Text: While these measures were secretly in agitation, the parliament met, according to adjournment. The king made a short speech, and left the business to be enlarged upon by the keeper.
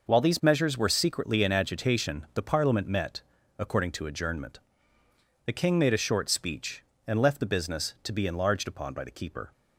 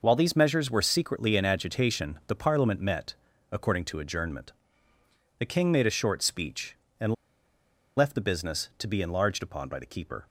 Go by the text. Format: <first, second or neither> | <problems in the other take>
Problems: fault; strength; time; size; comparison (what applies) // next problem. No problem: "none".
first | pauses between "and" and "left"; noticeable; at 7.1 s; 0.82 s long